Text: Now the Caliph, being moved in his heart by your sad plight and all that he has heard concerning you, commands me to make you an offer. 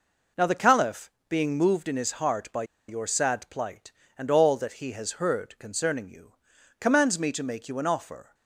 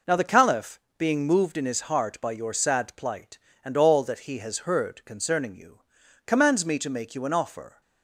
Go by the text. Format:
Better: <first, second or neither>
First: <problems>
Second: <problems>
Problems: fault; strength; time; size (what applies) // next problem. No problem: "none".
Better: second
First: pauses between "by" and "your"; slight; at 2.6 s; 0.24 s long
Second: none